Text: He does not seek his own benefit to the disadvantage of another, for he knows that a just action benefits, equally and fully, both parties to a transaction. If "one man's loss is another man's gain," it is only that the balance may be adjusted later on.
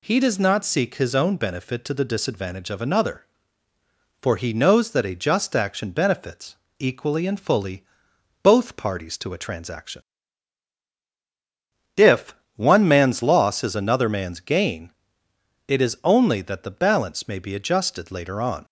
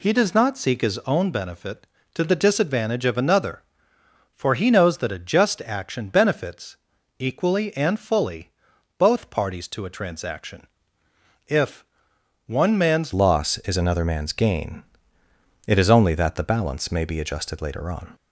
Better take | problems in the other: first | pauses between "If" and "one"; noticeable; at 11.8 s; 0.62 s long; slight in the first // changes voice at "loss"; from 13.1 s on; 5.0 s long

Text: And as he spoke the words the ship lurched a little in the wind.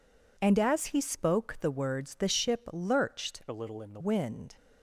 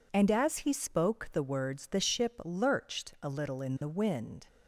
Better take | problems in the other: second | changes voice from "a" to "the"; from 3.4 to 3.9 s; 0.5 s long

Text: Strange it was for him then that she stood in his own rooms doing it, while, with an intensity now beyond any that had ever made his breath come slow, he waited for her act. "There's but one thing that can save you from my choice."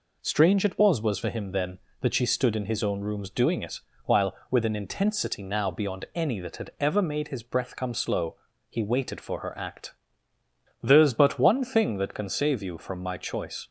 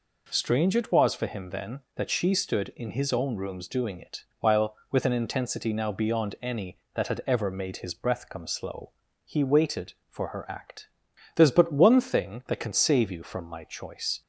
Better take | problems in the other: second | says "was" twice; at 1.0 s

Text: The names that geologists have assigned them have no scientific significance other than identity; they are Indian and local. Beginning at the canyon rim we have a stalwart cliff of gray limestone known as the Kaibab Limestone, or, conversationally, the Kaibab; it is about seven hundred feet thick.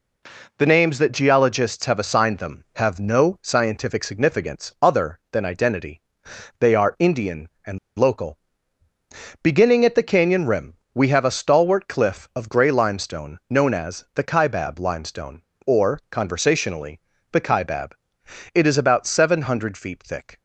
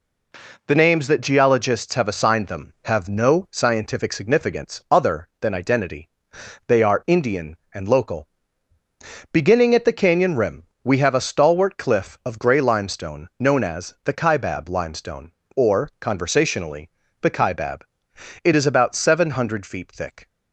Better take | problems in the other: second | pauses between "and" and "local"; slight; at 7.7 s; 0.20 s long // pauses between "rim" and "we"; slight; at 10.7 s; 0.18 s long; slight in the second

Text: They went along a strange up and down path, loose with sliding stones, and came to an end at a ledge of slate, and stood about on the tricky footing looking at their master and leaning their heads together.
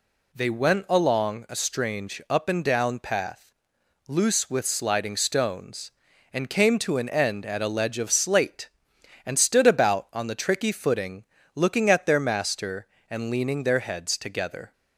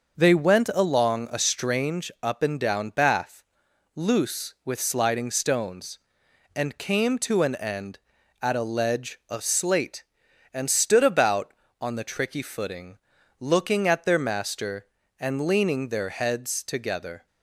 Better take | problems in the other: first | starts louder than the rest; noticeable; until 1.2 s; 6 dB // says "bath" for "path"; at 2.9 s // pauses between "footing" and "looking"; at 12.9 s; 0.40 s long; slight in the first

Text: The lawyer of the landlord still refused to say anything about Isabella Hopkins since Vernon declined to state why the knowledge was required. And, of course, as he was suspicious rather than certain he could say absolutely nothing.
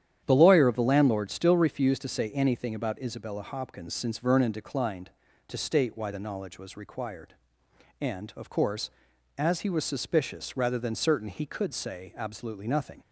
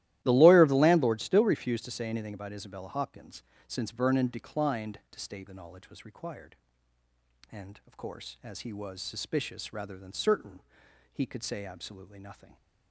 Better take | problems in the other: first | starts louder than the rest; strong; until 1.2 s; 14.5 dB; strong in the first // pauses between "Hopkins" and "since"; slight; at 3.4 s; 0.26 s long // skips "why"; at 5.4 s // pauses between "certain" and "he"; noticeable; at 10.5 s; 0.52 s long

